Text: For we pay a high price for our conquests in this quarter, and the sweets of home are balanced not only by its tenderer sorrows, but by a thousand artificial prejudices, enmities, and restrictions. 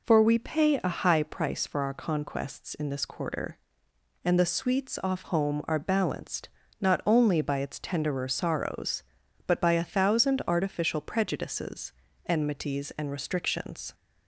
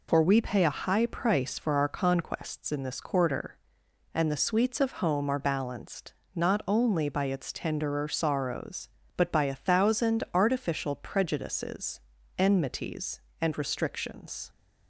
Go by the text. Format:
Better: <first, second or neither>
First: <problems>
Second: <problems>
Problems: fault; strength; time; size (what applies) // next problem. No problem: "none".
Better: second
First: says "off" for "of"; at 5.0 s // pauses between "balanced" and "not"; slight; at 6.4 s; 0.32 s long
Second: pauses between "balanced" and "not"; slight; at 6.1 s; 0.20 s long